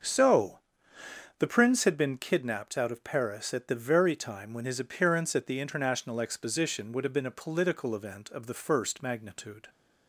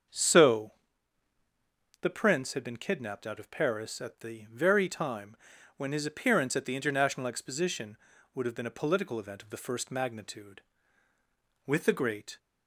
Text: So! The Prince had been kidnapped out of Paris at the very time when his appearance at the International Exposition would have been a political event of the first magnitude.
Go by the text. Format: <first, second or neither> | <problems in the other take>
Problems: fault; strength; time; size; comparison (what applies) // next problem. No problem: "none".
first | starts louder than the rest; strong; until 2.3 s; 7 dB; also in the first // pauses between "time" and "when"; at 5.3 s; 0.40 s long // goes on to say "With the Great"; noticeable; from 11.6 s on; 0.72 s long